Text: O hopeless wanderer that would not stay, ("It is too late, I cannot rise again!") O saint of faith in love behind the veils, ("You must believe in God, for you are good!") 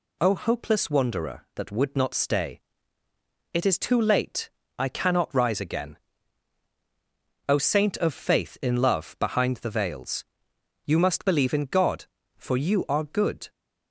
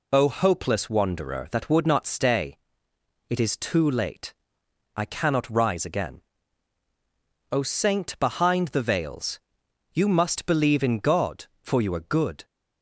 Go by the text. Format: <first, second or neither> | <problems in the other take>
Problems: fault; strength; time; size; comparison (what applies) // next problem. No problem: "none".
first | skips "of faith in love"; at 8.1 s